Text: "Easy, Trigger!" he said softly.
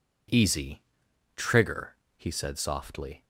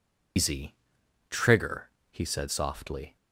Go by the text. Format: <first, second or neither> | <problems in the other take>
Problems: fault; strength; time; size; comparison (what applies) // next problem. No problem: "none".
first | loses the start of "Easy"; at 0.3 s; 150 ms